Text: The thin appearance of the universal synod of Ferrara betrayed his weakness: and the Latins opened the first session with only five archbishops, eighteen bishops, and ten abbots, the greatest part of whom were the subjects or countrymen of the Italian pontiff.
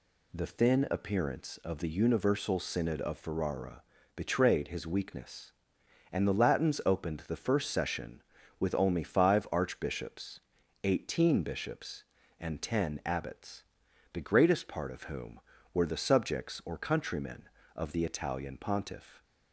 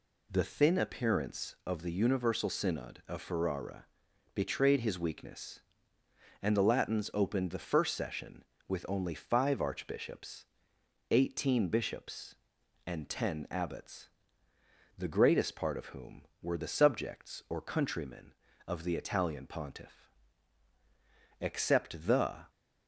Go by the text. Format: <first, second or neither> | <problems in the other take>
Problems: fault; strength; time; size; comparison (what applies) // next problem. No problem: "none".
first | pauses between "Ferrara" and "betrayed"; noticeable; at 3.8 s; 0.50 s long; slight in the first // goes on to say "Except the"; noticeable; from 21.3 s on; 1.1 s long